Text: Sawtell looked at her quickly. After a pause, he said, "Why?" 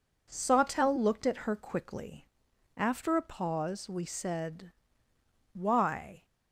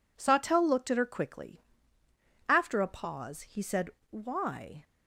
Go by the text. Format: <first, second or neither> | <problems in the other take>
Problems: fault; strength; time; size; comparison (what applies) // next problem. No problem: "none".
second | says "we" for "he"; at 3.8 s